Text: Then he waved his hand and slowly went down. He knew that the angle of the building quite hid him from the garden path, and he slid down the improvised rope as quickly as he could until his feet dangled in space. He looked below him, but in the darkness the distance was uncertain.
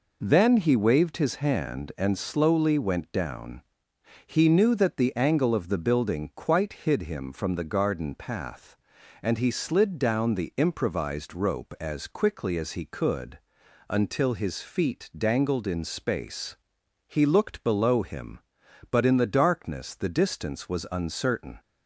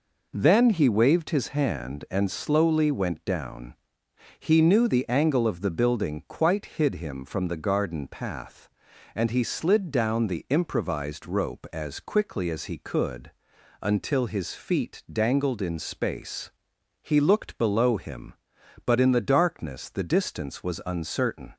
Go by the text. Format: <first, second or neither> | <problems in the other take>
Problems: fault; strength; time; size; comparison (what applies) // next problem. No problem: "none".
first | skips "that"; at 4.8 s // pauses between "could" and "until"; noticeable; at 13.3 s; 0.50 s long; noticeable in the first